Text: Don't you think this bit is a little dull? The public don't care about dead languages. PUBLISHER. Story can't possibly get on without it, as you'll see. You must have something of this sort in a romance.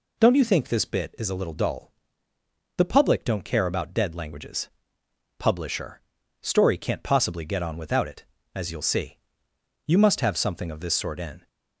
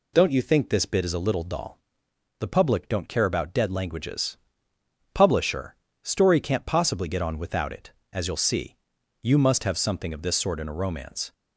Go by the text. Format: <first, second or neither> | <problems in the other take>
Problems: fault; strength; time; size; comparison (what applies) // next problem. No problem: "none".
second | stops before "a romance"; at 11.4 s